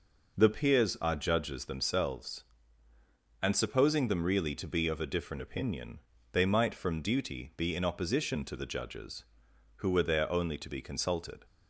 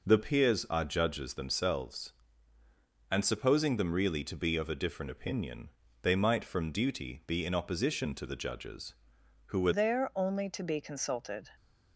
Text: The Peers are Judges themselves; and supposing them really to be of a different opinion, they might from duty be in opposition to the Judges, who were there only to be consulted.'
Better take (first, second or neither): first